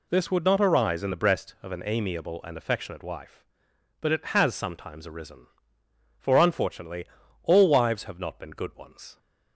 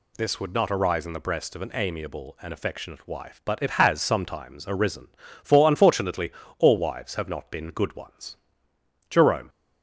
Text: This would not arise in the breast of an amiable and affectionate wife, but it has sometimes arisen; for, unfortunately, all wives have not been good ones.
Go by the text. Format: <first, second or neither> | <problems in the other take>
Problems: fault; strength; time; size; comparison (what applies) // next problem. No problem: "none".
first | goes on to say "Jerome"; slight; from 9.0 s on; 0.40 s long